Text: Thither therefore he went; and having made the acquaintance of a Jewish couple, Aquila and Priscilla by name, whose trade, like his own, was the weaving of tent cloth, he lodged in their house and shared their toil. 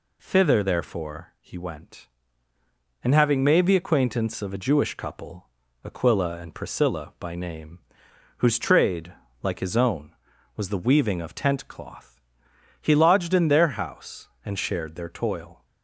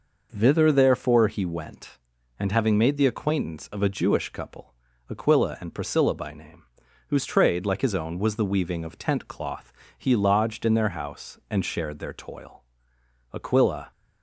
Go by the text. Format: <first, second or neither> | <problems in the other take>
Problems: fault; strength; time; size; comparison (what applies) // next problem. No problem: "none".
first | goes on to say "Aquila"; from 13.3 s on; 0.56 s long